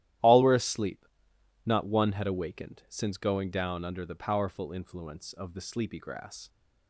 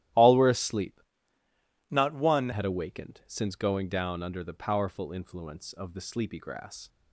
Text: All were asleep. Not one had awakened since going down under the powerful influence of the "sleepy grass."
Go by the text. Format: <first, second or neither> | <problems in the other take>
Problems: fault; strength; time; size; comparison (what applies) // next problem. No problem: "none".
first | starts louder than the rest; strong; until 2.0 s; 13.5 dB; strong in the first // changes voice from "Not" to "one"; from 1.9 to 2.5 s; 0.6 s long